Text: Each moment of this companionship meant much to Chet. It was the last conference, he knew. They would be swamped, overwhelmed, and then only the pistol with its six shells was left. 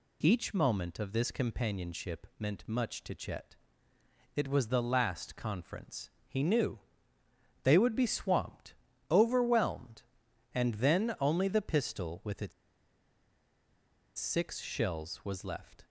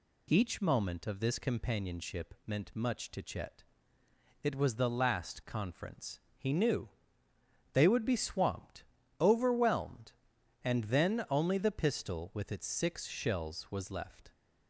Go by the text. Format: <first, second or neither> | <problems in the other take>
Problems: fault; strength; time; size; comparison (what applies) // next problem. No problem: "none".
second | pauses between "its" and "six"; strong; at 12.5 s; 1.6 s long